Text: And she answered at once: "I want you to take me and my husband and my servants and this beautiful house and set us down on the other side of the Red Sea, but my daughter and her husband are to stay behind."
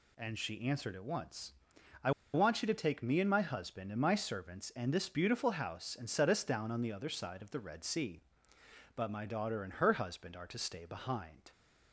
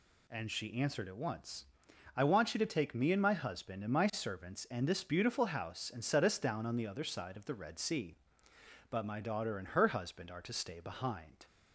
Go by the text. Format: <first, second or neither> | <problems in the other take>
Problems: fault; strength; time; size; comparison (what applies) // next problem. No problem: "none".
second | pauses between "I" and "want"; slight; at 2.1 s; 0.23 s long